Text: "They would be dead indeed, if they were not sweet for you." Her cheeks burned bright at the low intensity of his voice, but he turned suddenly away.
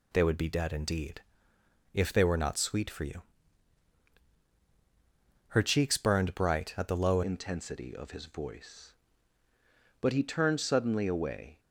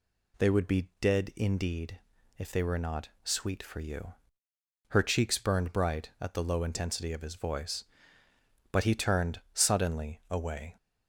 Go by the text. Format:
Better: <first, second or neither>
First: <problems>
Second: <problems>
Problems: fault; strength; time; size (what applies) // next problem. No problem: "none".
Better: second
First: changes voice at "intensity"; from 7.2 s on; 4.3 s long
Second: none